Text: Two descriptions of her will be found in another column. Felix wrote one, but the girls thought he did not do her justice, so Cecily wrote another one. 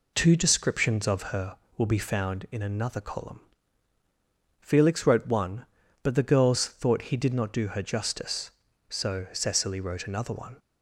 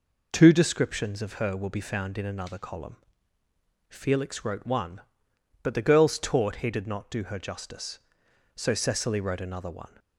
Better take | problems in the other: first | says "taught" for "thought"; at 6.1 s

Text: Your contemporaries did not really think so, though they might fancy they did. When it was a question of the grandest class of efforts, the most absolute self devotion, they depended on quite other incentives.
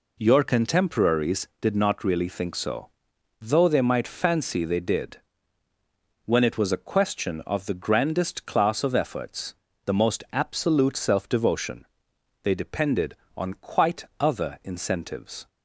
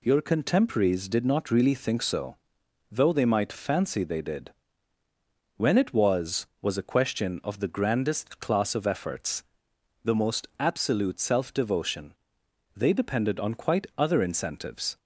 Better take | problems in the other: first | says "was" twice; at 6.6 s

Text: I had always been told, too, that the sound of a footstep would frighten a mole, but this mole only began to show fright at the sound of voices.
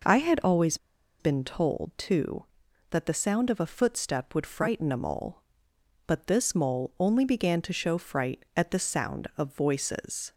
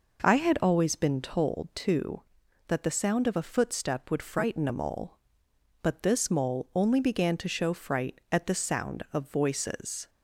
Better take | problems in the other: second | pauses between "always" and "been"; at 0.7 s; 0.43 s long

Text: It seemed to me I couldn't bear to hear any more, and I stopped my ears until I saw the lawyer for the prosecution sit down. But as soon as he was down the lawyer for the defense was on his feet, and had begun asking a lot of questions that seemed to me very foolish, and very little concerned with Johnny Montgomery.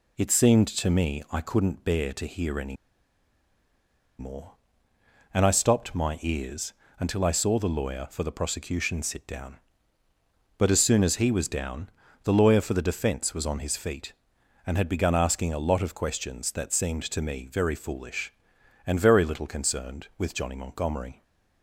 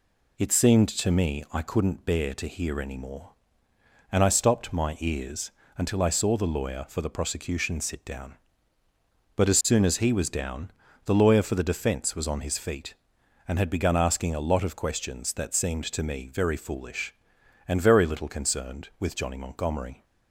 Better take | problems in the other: second | pauses between "any" and "more"; strong; at 2.7 s; 1.4 s long // pauses between "ears" and "until"; slight; at 6.7 s; 0.26 s long; slight in the second // pauses between "down" and "the"; slight; at 11.9 s; 0.34 s long; slight in the second

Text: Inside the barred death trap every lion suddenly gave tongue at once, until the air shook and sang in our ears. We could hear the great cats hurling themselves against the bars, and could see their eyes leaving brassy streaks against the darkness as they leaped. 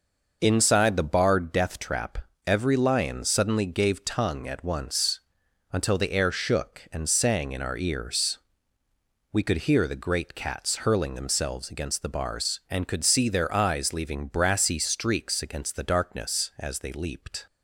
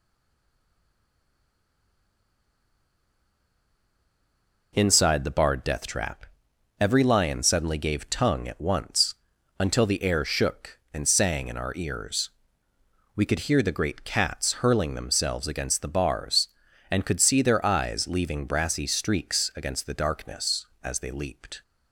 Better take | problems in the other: first | stays silent before the first word; strong; until 4.7 s; 4.7 s long // pauses between "trap" and "every"; noticeable; at 6.2 s; 0.54 s long; slight in the first

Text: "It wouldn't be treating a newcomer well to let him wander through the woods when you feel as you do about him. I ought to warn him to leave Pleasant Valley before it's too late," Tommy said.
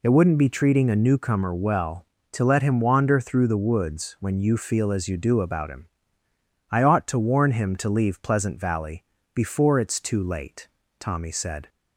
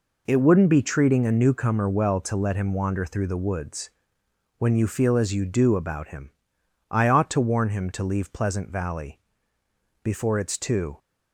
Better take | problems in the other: first | pauses between "woods" and "when"; noticeable; at 3.9 s; 0.68 s long // pauses between "Valley" and "before"; noticeable; at 9.2 s; 0.82 s long; slight in the first // stops before "late Tommy said"; at 10.9 s

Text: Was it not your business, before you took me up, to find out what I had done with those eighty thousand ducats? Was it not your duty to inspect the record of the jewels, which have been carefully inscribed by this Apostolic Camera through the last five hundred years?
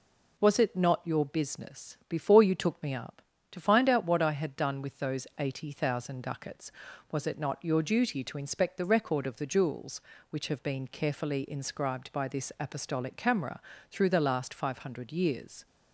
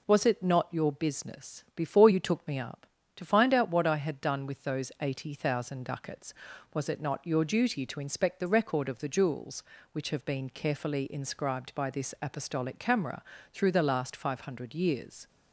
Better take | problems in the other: neither | pauses between "Camera" and "through"; slight; the same in both

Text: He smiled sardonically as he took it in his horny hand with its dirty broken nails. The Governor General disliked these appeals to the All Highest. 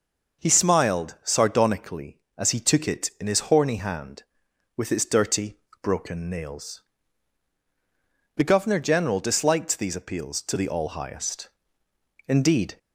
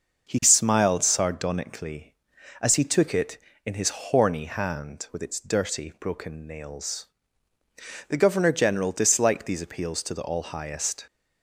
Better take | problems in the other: second | pauses between "dirty" and "broken"; slight; at 5.5 s; 0.26 s long // goes on to say "Indeed"; from 12.2 s on; 0.50 s long

